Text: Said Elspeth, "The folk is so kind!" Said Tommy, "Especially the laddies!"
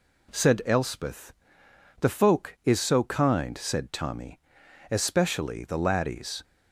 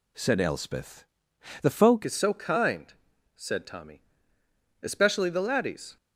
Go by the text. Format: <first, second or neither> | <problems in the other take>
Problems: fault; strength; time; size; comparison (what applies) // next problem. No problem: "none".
first | changes voice at "is"; from 2.0 s on; 3.9 s long